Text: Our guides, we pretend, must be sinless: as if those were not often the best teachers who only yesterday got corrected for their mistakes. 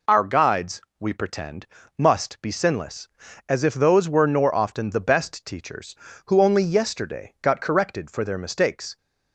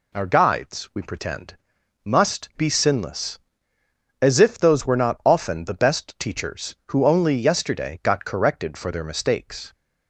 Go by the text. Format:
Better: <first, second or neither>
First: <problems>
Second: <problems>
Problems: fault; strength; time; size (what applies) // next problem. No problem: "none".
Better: second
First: says "nor" for "not"; at 4.2 s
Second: none